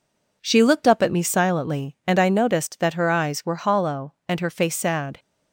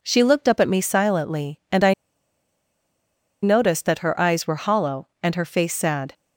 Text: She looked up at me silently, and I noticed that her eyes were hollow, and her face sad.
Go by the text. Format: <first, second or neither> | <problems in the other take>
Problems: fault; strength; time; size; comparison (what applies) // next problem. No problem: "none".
first | pauses between "I" and "noticed"; strong; at 1.9 s; 1.5 s long